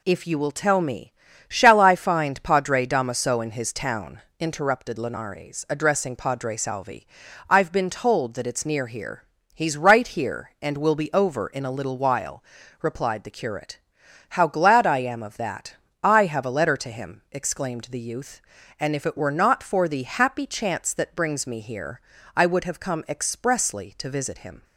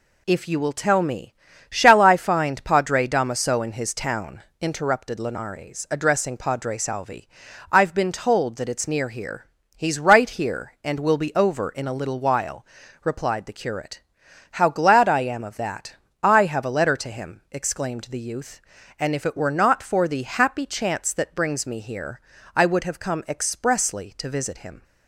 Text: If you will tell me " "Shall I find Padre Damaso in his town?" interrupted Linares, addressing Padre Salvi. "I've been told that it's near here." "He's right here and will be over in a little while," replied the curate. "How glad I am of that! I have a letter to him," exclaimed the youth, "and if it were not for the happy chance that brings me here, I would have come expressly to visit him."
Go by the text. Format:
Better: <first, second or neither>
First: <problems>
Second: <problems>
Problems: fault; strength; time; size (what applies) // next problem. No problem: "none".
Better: neither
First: none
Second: none